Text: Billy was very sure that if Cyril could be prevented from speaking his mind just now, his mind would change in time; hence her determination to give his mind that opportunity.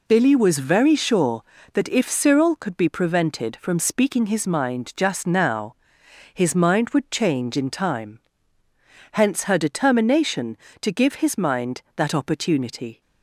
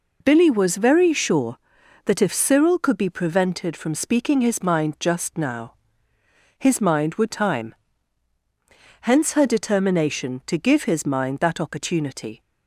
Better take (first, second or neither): first